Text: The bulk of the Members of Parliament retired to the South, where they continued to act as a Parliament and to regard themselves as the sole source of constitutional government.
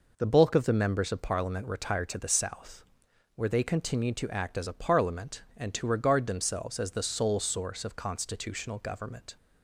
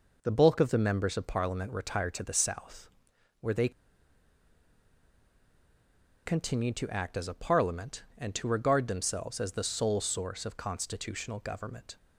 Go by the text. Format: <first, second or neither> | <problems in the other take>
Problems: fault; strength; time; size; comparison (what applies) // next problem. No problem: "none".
first | pauses between "they" and "continued"; strong; at 3.6 s; 2.5 s long